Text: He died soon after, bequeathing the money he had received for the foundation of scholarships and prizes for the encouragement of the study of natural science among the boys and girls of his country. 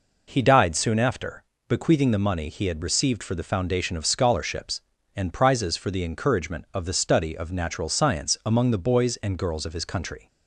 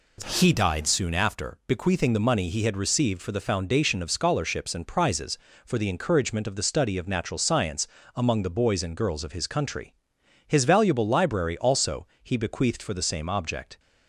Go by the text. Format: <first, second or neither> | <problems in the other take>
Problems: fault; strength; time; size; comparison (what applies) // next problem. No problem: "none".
first | pauses between "science" and "among"; slight; at 7.8 s; 0.28 s long // goes on to say "His valuable library also he bequeathed for the same object"; strong; from 10.4 s on; 3.3 s long